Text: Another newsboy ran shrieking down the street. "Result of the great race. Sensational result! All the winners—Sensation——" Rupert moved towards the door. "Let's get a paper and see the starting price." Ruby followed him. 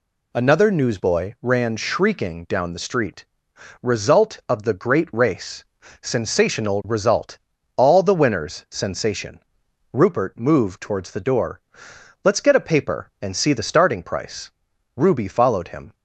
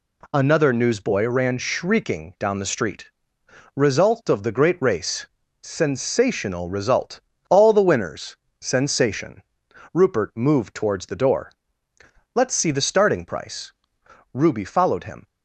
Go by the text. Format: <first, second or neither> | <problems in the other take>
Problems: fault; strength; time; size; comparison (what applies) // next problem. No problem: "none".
first | skips "get a paper and"; at 12.5 s